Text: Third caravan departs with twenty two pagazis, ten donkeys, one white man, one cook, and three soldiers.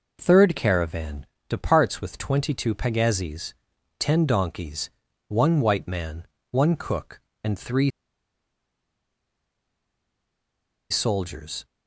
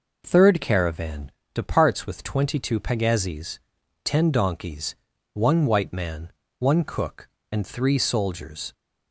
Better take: second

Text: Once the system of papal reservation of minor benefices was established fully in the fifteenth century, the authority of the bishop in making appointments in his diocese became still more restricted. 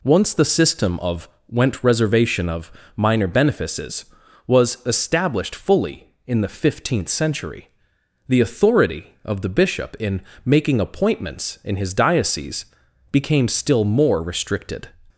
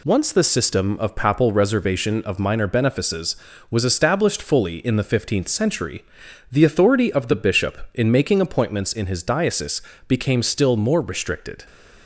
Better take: second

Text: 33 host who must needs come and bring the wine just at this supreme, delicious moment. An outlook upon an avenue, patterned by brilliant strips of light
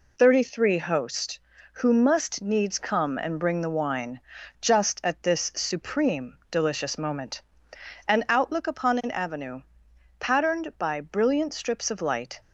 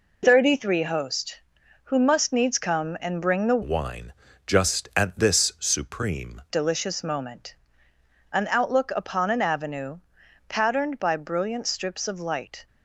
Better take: first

